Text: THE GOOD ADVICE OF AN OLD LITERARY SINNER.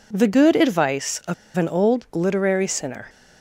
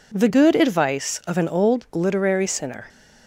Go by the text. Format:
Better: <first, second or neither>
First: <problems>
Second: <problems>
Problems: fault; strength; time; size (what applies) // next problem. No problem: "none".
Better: second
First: pauses between "OF" and "AN"; slight; at 1.3 s; 0.22 s long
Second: none